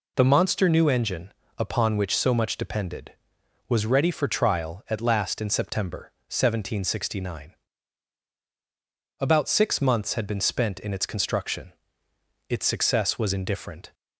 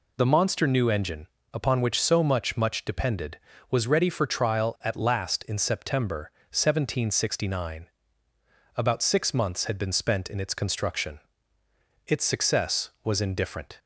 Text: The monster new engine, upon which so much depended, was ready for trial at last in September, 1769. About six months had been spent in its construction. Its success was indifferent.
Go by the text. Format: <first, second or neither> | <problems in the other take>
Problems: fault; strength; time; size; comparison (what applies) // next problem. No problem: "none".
first | says "much" twice; at 2.5 s